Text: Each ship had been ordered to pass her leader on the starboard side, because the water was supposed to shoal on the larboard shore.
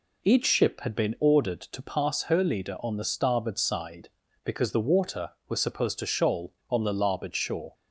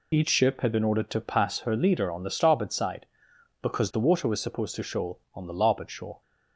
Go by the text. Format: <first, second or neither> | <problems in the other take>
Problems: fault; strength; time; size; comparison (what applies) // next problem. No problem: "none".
neither | none